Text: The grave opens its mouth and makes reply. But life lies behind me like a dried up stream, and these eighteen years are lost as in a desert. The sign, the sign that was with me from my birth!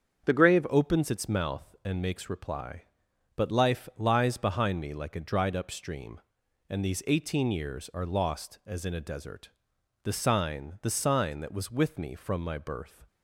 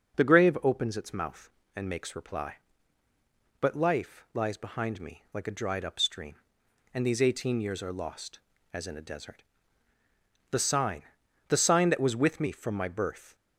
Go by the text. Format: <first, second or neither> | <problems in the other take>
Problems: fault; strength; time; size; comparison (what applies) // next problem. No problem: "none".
second | starts louder than the rest; strong; until 1.2 s; 7 dB // changes voice at "opens"; from 0.7 s on; 12.3 s long